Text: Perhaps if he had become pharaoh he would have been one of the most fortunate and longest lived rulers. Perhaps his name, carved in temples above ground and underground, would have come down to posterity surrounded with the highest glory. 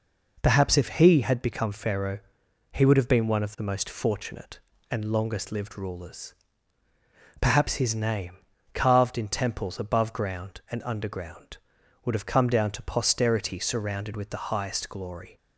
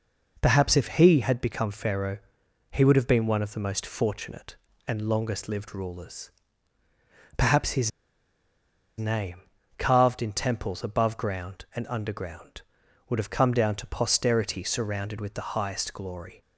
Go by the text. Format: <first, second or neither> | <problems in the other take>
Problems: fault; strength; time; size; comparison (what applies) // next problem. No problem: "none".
first | pauses between "pharaoh" and "he"; noticeable; at 2.1 s; 0.52 s long; noticeable in the first // pauses between "his" and "name"; at 7.8 s; 1.0 s long